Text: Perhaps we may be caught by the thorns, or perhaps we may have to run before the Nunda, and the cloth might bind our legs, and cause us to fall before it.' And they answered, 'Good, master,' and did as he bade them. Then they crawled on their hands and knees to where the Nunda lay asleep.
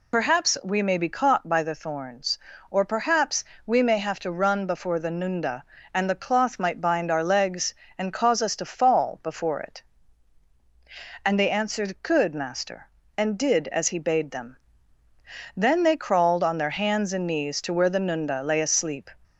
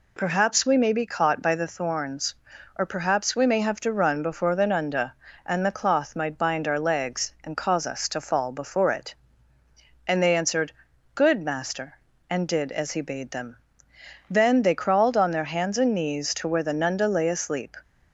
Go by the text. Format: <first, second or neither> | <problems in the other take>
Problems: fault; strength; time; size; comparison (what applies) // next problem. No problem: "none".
second | loses the start of "Perhaps"; at 0.1 s; 60 ms // pauses between "perhaps" and "we"; slight; at 3.4 s; 0.22 s long